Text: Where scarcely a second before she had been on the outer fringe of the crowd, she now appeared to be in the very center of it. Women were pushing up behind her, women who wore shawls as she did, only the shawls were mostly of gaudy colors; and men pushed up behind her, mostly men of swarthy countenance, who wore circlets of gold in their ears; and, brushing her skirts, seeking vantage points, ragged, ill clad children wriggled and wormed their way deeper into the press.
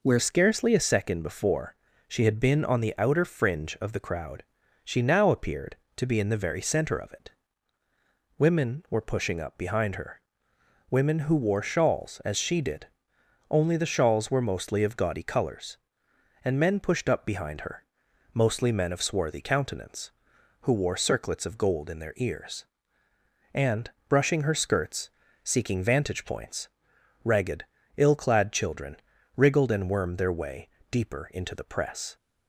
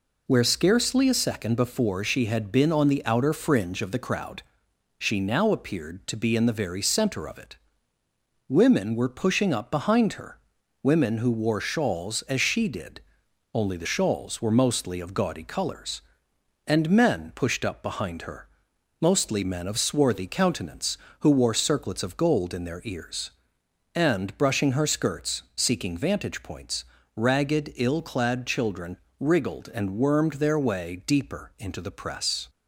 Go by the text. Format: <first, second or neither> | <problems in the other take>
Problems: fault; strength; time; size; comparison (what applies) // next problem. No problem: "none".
second | changes voice at "scarcely"; from 0.1 s on; 32.0 s long // pauses between "before" and "she"; slight; at 1.7 s; 0.32 s long // pauses between "children" and "wriggled"; at 28.9 s; 0.38 s long; slight in the second // pauses between "way" and "deeper"; slight; at 30.6 s; 0.24 s long